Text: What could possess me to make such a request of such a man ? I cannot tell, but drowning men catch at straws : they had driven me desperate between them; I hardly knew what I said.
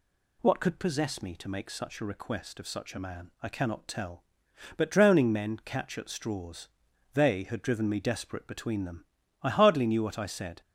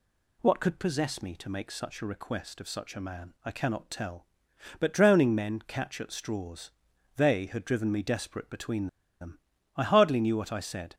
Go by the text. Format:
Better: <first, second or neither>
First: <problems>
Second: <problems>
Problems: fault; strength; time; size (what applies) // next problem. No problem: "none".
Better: first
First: none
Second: pauses between "between" and "them"; slight; at 8.8 s; 0.33 s long